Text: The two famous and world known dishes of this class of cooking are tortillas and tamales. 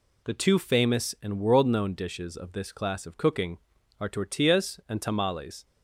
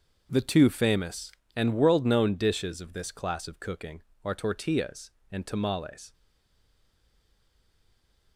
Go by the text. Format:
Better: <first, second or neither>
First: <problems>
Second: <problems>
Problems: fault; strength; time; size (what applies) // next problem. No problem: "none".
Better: first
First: none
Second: starts louder than the rest; until 1.3 s; 6.5 dB // stays silent after the last word; from 6.1 s on; 2.2 s long